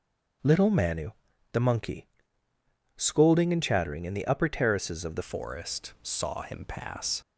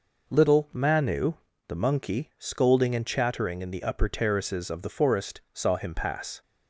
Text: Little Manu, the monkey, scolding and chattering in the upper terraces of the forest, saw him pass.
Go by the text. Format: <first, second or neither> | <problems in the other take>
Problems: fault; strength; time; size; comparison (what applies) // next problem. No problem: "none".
second | starts louder than the rest; until 1.8 s; 7 dB // changes voice at "forest"; from 5.2 s on; 2.0 s long